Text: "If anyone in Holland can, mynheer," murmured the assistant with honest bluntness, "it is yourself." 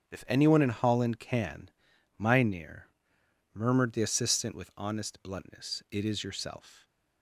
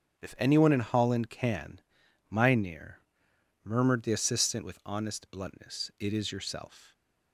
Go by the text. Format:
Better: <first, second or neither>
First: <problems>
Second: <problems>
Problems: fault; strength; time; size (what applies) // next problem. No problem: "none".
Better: neither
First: starts louder than the rest; strong; until 1.1 s; 7.5 dB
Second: starts louder than the rest; strong; until 1.2 s; 7.5 dB